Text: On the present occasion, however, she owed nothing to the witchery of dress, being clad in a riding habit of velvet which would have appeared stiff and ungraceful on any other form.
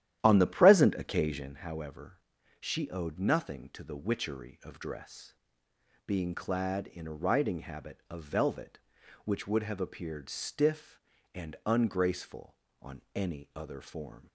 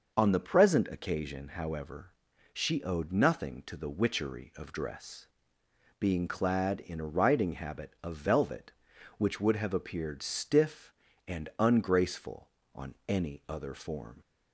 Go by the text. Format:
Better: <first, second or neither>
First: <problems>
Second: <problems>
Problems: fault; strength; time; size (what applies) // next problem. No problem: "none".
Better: second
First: starts louder than the rest; strong; until 1.6 s; 11.5 dB // pauses between "on" and "any"; slight; at 12.9 s; 0.16 s long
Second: pauses between "on" and "any"; slight; at 12.9 s; 0.16 s long